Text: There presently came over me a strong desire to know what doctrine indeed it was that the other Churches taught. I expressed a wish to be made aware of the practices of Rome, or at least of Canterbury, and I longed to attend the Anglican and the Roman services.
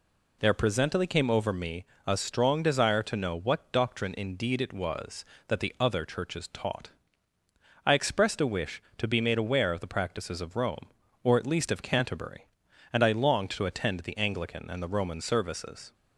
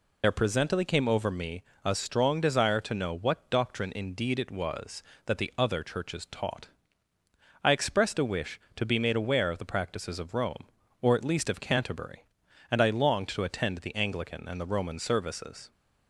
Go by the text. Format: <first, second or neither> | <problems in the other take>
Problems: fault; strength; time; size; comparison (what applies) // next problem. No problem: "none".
first | loses the start of "There"; at 0.2 s; 55 ms // pauses between "me" and "a"; slight; at 1.6 s; 0.22 s long; slight in the first